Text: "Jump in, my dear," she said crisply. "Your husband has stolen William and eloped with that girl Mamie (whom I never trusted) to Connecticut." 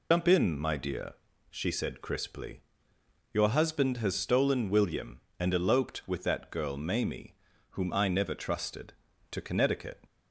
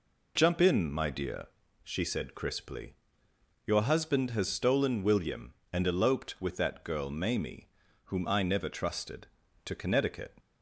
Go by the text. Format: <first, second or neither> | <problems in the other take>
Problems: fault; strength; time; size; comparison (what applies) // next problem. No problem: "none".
second | loses the start of "Jump"; at 0.1 s; 85 ms